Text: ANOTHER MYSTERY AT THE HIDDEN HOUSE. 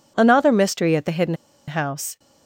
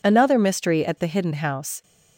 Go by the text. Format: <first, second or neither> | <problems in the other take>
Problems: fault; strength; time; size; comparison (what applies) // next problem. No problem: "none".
second | pauses between "HIDDEN" and "HOUSE"; slight; at 1.3 s; 0.34 s long